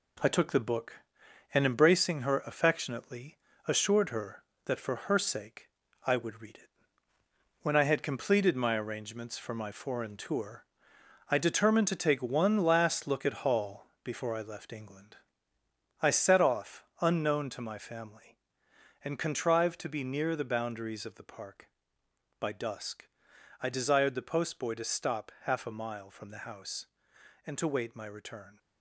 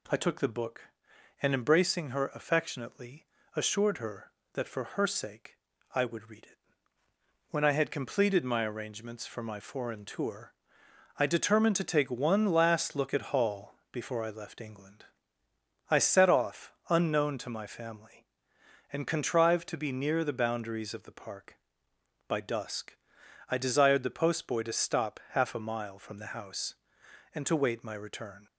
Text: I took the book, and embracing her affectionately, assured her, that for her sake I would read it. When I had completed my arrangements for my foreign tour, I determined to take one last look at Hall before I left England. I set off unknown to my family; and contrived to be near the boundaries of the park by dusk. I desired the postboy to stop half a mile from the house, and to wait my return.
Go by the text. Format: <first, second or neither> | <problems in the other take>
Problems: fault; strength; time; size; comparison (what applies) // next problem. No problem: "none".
second | gets quieter; noticeable; throughout; 6 dB // pauses between "sake" and "I"; at 5.6 s; 0.38 s long; also in the second // pauses between "Hall" and "before"; slight; at 13.8 s; 0.18 s long; slight in the second // pauses between "off" and "unknown"; slight; at 16.8 s; 0.16 s long; slight in the second